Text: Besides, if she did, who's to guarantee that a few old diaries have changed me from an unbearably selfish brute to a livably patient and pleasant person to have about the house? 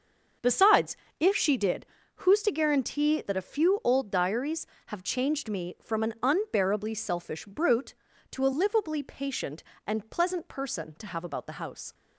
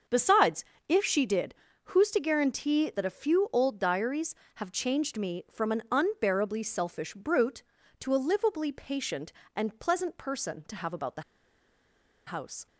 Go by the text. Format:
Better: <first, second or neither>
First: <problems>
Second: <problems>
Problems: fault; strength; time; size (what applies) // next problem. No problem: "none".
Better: first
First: starts louder than the rest; until 1.6 s; 6.5 dB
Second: starts louder than the rest; until 1.3 s; 6.5 dB // pauses between "the" and "house"; at 11.2 s; 1.0 s long